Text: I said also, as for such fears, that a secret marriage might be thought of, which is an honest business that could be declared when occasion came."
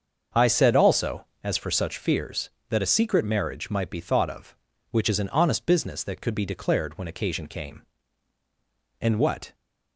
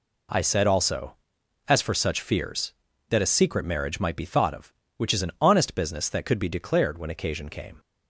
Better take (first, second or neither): second